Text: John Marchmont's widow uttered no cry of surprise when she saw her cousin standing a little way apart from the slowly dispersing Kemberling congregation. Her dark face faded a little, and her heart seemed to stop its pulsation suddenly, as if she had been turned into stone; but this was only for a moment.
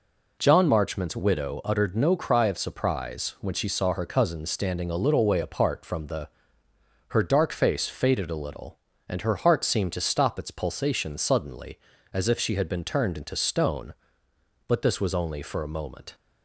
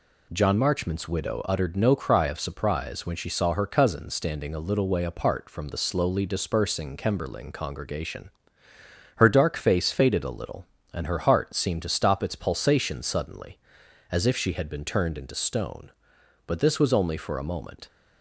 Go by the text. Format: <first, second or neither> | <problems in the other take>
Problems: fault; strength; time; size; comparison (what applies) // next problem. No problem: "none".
second | skips "slowly dispersing Kemberling congregation"; at 6.6 s